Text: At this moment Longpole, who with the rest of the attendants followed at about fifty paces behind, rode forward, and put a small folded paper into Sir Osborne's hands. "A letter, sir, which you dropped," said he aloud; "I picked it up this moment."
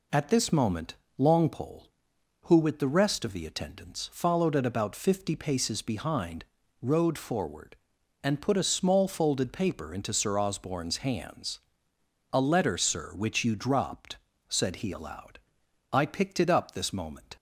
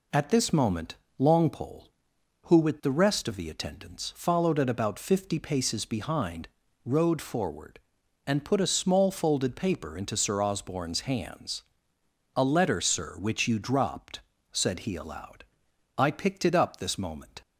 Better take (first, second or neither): neither